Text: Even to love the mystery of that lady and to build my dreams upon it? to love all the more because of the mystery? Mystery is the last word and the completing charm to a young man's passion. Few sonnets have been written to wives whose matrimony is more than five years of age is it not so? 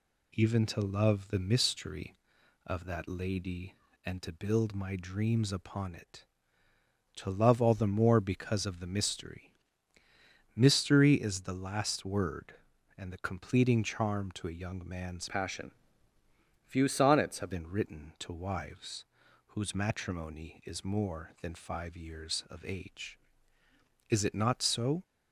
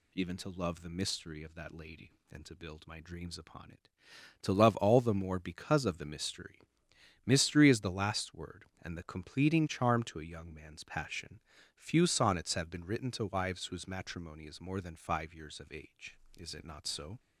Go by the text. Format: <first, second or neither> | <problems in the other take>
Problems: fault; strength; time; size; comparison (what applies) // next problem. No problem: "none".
second | changes voice from "passion" to "have"; from 15.2 to 17.4 s; 2.2 s long // pauses between "wives" and "whose"; at 19.0 s; 0.40 s long